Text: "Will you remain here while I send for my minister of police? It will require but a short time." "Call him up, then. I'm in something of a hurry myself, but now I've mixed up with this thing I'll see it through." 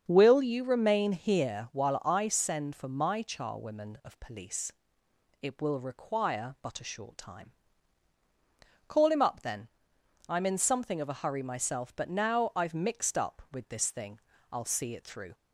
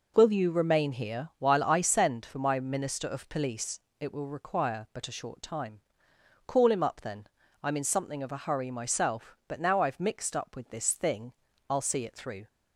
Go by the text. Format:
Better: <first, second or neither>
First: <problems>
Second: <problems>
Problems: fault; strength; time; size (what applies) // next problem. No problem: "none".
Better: second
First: starts louder than the rest; strong; until 1.0 s; 7 dB // says "charwomen" for "minister"; at 3.2 s // pauses between "thing" and "I'll"; slight; at 14.1 s; 0.32 s long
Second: pauses between "thing" and "I'll"; slight; at 11.3 s; 0.36 s long